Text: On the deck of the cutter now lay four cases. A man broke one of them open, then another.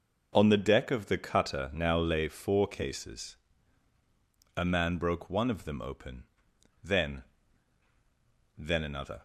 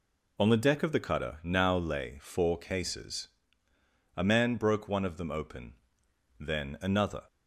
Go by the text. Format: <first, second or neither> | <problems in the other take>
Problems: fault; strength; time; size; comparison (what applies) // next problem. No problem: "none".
second | says "then" twice; at 8.5 s